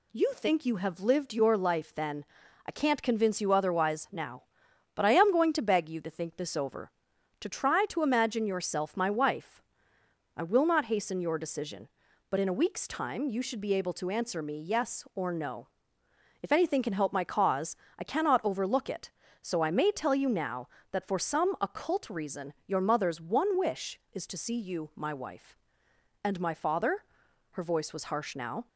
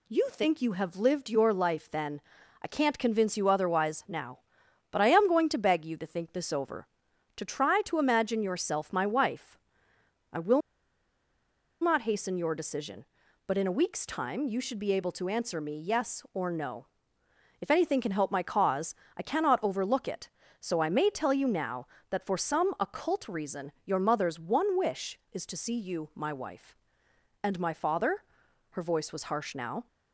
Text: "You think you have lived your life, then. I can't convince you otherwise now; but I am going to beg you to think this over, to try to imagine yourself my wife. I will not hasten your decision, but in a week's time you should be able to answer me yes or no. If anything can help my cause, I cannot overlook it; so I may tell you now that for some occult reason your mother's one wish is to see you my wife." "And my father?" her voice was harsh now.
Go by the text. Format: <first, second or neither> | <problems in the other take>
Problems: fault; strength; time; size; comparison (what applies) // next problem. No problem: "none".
first | pauses between "will" and "not"; at 10.6 s; 1.2 s long